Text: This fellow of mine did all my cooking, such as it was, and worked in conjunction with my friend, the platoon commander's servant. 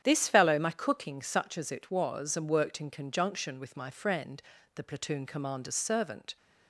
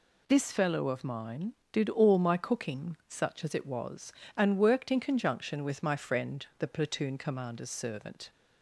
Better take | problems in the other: second | starts louder than the rest; strong; until 1.0 s; 9.5 dB // skips "of mine did all"; at 0.6 s

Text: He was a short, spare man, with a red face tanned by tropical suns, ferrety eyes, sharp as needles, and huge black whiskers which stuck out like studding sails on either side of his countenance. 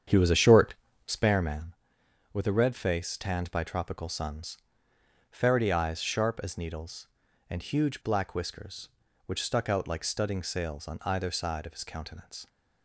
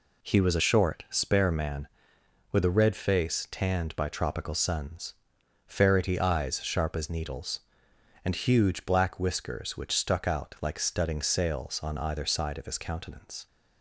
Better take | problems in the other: second | starts louder than the rest; strong; until 1.3 s; 8 dB

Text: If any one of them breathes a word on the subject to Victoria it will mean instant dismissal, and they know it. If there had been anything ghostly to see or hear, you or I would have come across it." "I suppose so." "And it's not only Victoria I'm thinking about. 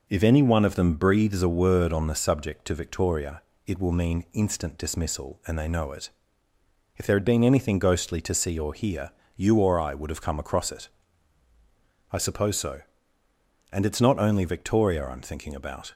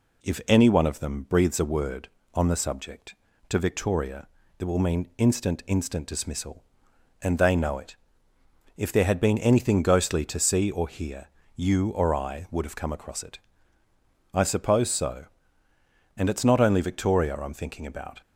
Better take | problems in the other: first | pauses between "Victoria" and "it"; slight; at 4.2 s; 0.32 s long; slight in the first // says "instant" twice; at 5.6 s

